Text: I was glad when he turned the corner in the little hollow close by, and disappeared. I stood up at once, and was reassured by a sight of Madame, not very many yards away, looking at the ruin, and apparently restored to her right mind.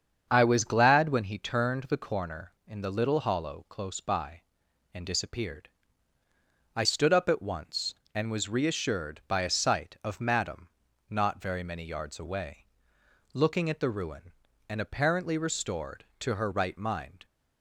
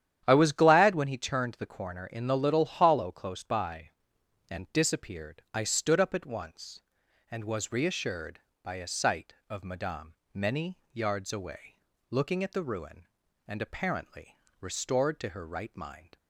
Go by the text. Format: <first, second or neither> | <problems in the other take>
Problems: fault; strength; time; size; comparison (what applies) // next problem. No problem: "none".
first | starts louder than the rest; strong; until 1.2 s; 10.5 dB; strong in the first // skips "not very"; at 10.2 s // pauses between "many" and "yards"; slight; at 10.7 s; 0.16 s long // pauses between "apparently" and "restored"; slight; at 14.3 s; 0.24 s long